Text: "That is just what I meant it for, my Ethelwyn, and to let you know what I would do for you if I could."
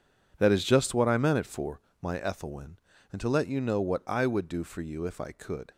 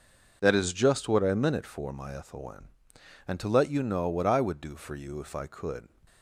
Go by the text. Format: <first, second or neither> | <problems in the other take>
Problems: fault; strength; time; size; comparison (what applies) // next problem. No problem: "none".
second | gets quieter; strong; throughout; 13 dB